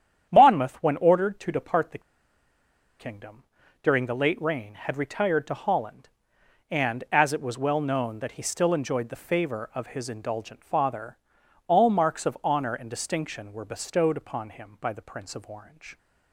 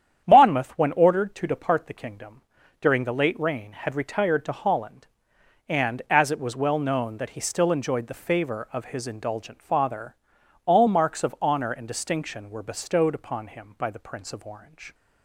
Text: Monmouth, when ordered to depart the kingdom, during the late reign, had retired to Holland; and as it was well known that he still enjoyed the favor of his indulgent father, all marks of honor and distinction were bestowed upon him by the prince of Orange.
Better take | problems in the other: second | starts louder than the rest; strong; until 1.3 s; 9.5 dB; strong in the second // pauses between "the" and "kingdom"; at 2.0 s; 0.98 s long

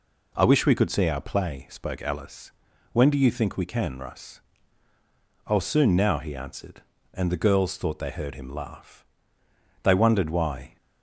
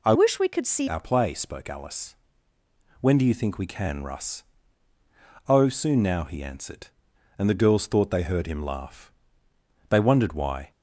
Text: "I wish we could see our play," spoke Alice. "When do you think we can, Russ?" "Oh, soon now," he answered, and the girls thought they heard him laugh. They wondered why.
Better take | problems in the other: first | changes voice from "wish" to "see"; from 0.1 to 0.8 s; 0.7 s long

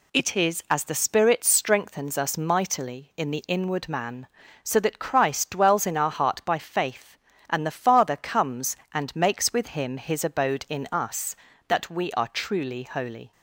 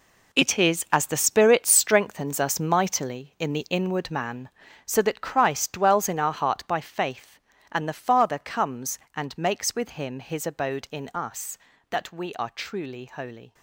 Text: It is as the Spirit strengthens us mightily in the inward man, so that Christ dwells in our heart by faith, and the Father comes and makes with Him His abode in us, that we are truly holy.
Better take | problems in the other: first | gets quieter; strong; throughout; 12 dB

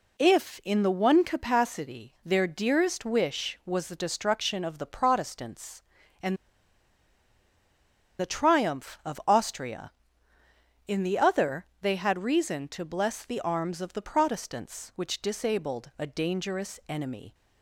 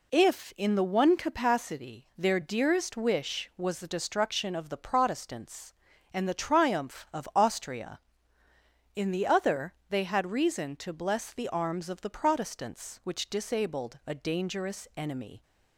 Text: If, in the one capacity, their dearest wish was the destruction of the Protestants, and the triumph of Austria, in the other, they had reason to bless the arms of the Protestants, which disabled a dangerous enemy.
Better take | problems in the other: second | pauses between "and" and "the"; strong; at 6.3 s; 1.8 s long

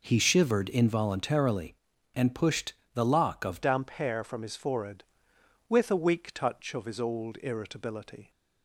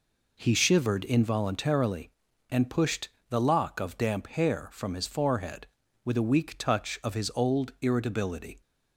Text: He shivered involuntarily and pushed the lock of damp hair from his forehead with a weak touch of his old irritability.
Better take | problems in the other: second | pauses between "pushed" and "the"; slight; at 2.7 s; 0.22 s long; slight in the second // changes voice at "damp"; from 3.6 s on; 4.7 s long

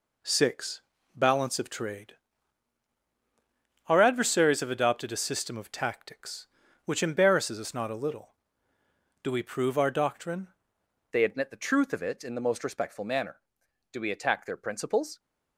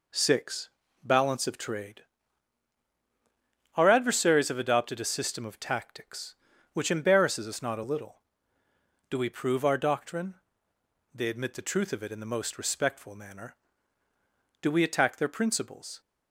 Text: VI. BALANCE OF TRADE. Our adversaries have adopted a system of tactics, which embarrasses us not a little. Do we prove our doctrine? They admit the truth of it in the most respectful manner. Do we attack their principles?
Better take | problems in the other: second | changes voice at "They"; from 11.1 s on; 4.0 s long

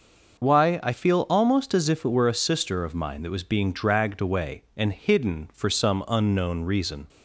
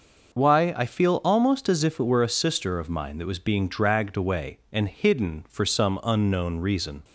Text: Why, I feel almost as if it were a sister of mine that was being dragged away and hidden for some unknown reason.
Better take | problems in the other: neither | none

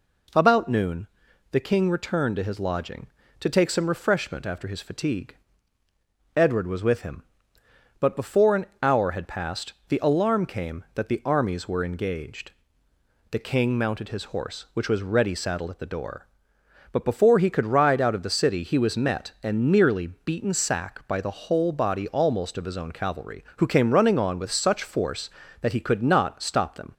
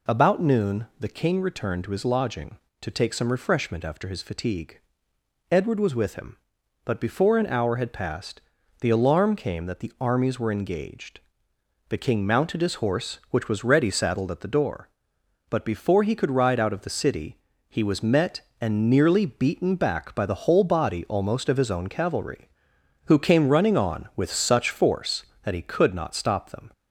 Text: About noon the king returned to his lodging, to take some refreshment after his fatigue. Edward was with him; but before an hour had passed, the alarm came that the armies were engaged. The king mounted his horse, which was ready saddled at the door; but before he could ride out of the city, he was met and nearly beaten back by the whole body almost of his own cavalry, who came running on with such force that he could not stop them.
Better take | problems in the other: second | pauses between "noon" and "the"; at 1.0 s; 0.44 s long // pauses between "an" and "hour"; slight; at 8.6 s; 0.16 s long // says "sack" for "back"; at 20.5 s

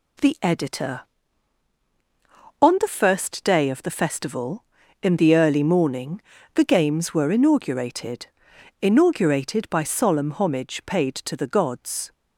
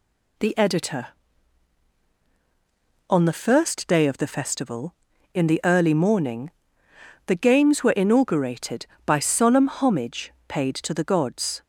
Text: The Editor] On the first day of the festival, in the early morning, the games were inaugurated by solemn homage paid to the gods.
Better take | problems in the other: second | says "inaugurated" twice; at 8.7 s

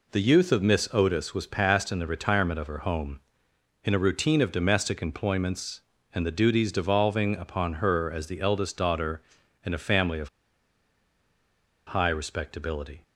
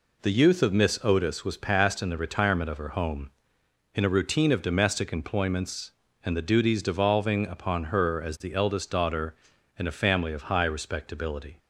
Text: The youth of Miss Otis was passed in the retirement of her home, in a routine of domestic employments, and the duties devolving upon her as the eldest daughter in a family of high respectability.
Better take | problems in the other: second | pauses between "of" and "high"; strong; at 10.2 s; 1.5 s long

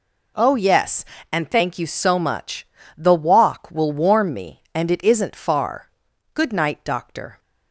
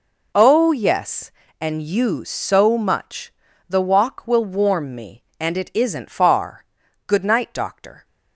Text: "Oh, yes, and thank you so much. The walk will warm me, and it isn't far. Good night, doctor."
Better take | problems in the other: first | skips "thank"; at 1.8 s

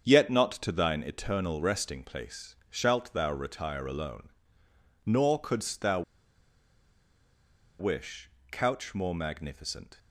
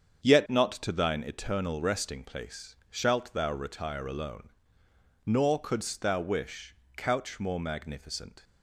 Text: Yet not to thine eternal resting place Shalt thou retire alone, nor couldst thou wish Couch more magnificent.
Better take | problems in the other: second | starts louder than the rest; strong; until 1.2 s; 7.5 dB; strong in the second // pauses between "thou" and "wish"; strong; at 6.0 s; 1.7 s long // pauses between "wish" and "Couch"; slight; at 8.3 s; 0.20 s long; slight in the second

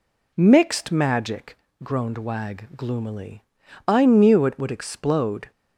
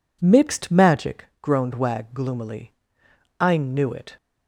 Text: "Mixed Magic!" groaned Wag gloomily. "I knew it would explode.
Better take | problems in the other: first | stops before "would explode"; at 4.1 s

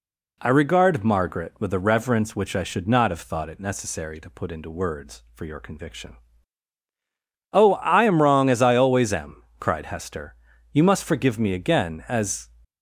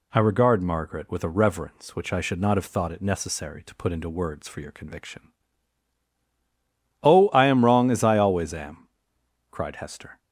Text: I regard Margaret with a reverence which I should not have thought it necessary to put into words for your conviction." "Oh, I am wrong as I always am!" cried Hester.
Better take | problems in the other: second | goes on to say "You must forgive me again as"; strong; from 10.7 s on; 1.7 s long

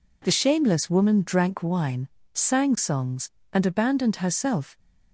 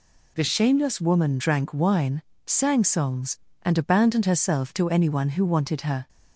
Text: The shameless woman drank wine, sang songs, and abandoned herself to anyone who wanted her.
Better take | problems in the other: second | stops before "to anyone who wanted her"; at 4.7 s

